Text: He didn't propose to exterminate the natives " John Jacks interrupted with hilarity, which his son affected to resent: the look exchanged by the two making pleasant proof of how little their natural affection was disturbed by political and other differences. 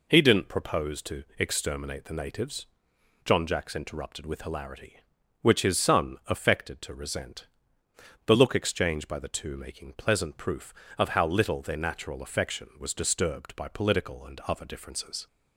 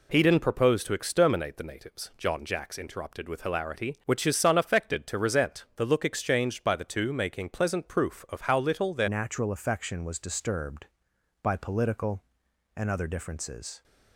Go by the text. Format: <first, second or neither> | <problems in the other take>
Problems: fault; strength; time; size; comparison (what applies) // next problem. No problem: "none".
first | changes voice at "natural"; from 9.0 s on; 4.8 s long